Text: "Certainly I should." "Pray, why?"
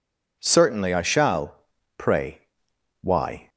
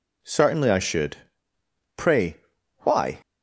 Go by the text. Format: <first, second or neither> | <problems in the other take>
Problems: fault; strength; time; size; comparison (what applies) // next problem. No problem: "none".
second | says "shall" for "should"; at 1.0 s